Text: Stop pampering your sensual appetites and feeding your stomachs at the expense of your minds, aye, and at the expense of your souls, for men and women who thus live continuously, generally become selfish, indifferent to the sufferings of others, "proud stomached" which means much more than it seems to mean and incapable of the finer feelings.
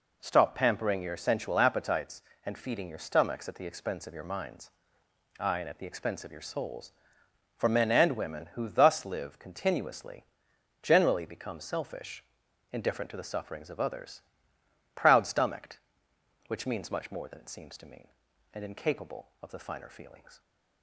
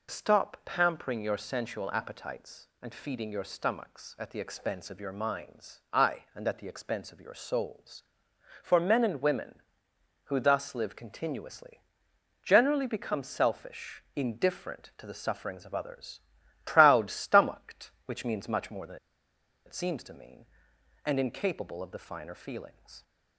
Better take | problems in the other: first | pauses between "than" and "it"; noticeable; at 18.9 s; 0.70 s long

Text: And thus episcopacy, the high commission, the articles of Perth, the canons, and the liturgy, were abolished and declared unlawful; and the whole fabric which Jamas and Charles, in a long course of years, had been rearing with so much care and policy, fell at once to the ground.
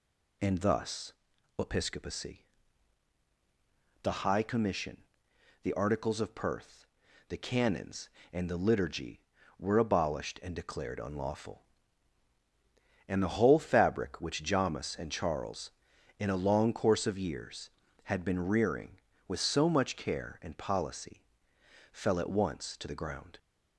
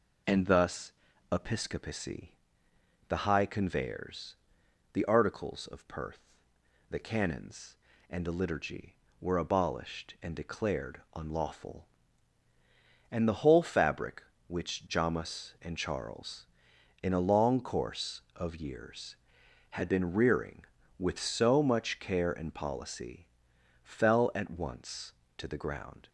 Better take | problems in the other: first | pauses between "thus" and "episcopacy"; at 0.9 s; 0.40 s long; also in the first // says "conveyors" for "commission"; at 3.4 s

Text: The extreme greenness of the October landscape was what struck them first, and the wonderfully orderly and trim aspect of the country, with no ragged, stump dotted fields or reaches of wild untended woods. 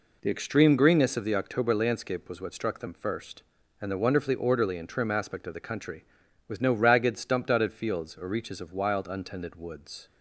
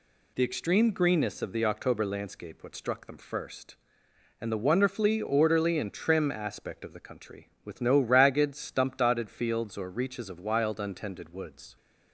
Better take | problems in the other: first | skips "was"; at 2.6 s

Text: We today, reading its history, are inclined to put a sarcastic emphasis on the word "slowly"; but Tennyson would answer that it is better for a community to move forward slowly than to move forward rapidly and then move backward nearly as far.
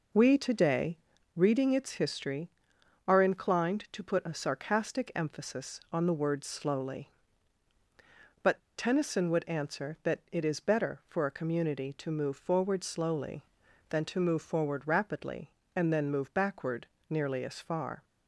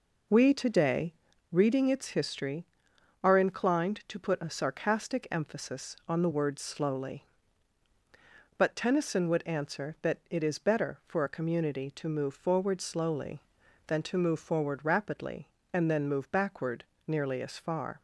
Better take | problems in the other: second | pauses between "but" and "Tennyson"; slight; at 8.6 s; 0.17 s long // pauses between "backward" and "nearly"; slight; at 16.8 s; 0.22 s long; slight in the second

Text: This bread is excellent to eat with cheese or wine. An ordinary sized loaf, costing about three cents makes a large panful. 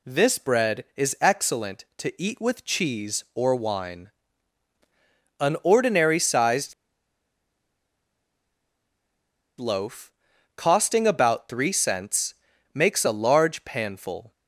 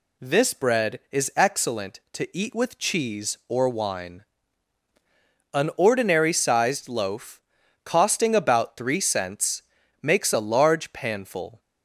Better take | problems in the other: second | pauses between "sized" and "loaf"; strong; at 6.7 s; 2.8 s long // pauses between "cents" and "makes"; at 12.3 s; 0.40 s long; also in the second

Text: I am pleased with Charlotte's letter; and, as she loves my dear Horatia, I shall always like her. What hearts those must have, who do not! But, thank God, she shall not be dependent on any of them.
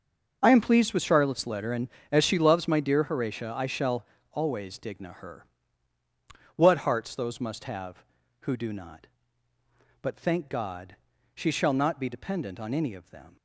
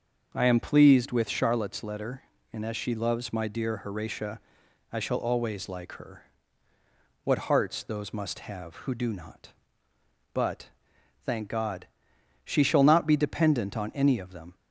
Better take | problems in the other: second | starts louder than the rest; until 1.4 s; 6.5 dB; also in the second // pauses between "shall" and "always"; slight; at 4.0 s; 0.26 s long // says "digna" for "like"; at 4.7 s

